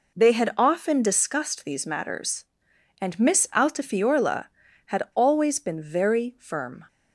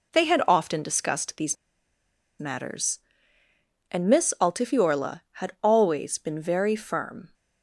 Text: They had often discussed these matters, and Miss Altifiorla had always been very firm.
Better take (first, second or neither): first